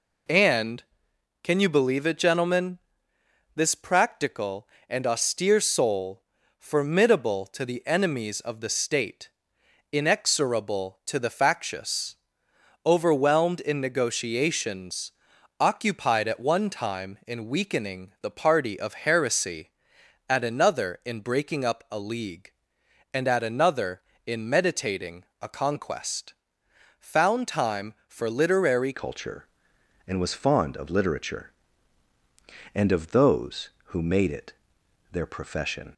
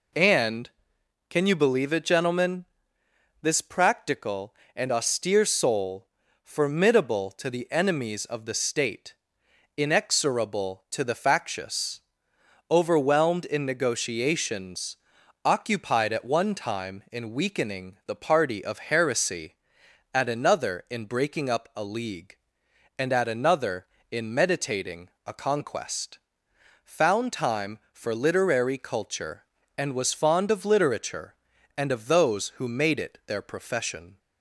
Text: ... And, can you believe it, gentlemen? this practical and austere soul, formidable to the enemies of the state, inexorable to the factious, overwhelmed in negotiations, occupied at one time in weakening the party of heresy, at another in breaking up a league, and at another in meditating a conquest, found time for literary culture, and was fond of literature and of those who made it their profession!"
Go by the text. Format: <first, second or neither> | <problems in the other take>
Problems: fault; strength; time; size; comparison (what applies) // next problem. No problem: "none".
second | pauses between "meditating" and "a"; slight; at 25.2 s; 0.18 s long; slight in the second // changes voice at "culture"; from 28.9 s on; 7.0 s long // pauses between "it" and "their"; noticeable; at 34.5 s; 0.58 s long